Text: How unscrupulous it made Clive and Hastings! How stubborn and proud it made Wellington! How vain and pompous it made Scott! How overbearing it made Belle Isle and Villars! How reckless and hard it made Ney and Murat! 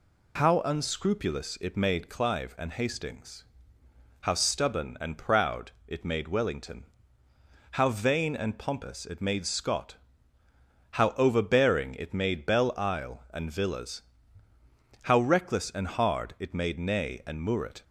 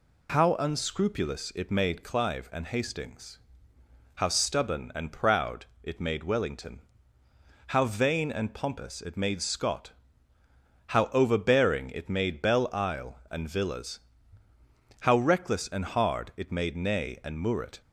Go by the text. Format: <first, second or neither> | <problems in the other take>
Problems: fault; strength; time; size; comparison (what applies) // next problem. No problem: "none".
neither | pauses between "proud" and "it"; slight; the same in both